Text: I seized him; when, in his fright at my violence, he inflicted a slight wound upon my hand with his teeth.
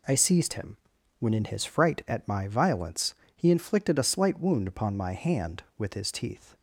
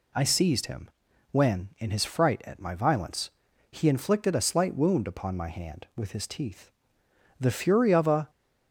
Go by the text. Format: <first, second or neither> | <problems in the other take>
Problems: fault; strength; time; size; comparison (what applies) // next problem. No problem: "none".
first | goes on to say "The fury of a"; noticeable; from 7.3 s on; 0.90 s long